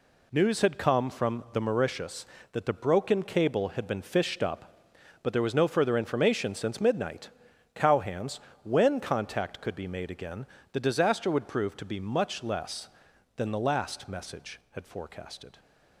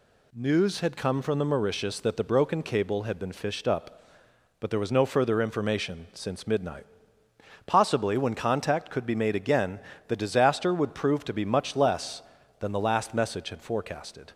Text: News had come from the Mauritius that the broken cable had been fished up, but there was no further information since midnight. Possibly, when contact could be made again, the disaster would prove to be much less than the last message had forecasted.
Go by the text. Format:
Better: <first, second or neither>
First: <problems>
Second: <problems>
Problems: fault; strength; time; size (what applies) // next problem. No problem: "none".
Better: second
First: says "Cowhands" for "Possibly"; at 7.7 s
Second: none